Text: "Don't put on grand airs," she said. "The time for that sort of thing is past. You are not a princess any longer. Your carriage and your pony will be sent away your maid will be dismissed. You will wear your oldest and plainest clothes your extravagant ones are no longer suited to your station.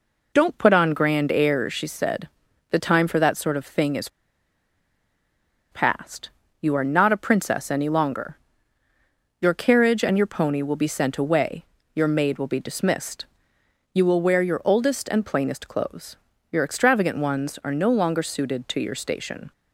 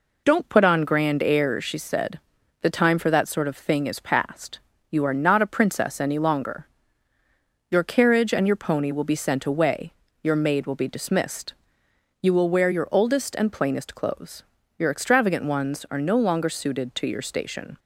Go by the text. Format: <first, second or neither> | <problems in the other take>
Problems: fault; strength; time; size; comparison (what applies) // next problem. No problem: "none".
second | pauses between "is" and "past"; strong; at 4.0 s; 1.6 s long // pauses between "away" and "your"; slight; at 11.6 s; 0.30 s long; slight in the second // pauses between "clothes" and "your"; slight; at 16.1 s; 0.34 s long; slight in the second